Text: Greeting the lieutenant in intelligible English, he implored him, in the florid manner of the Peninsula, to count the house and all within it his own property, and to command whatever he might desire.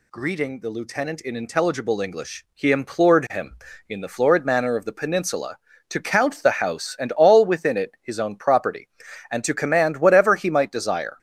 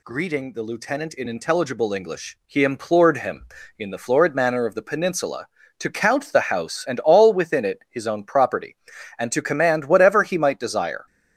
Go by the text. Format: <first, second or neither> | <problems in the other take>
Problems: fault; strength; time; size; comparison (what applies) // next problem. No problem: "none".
neither | none